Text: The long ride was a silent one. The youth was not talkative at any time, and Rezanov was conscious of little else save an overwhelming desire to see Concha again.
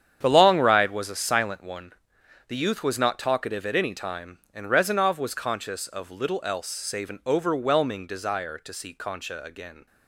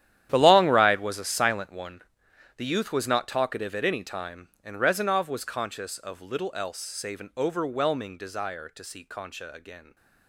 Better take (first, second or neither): first